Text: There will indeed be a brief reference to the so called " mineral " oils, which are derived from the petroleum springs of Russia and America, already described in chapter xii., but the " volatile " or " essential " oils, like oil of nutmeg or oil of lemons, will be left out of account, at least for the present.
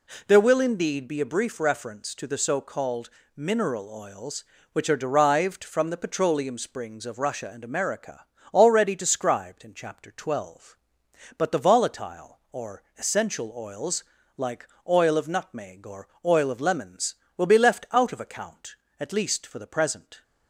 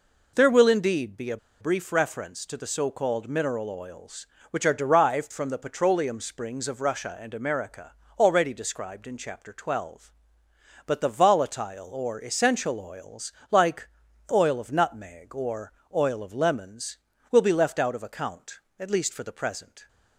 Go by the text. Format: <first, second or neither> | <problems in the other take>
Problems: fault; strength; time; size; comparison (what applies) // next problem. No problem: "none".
first | pauses between "a" and "brief"; slight; at 1.3 s; 0.24 s long // pauses between "like" and "oil"; at 13.8 s; 0.42 s long; slight in the first // pauses between "or" and "oil"; slight; at 15.7 s; 0.20 s long; slight in the first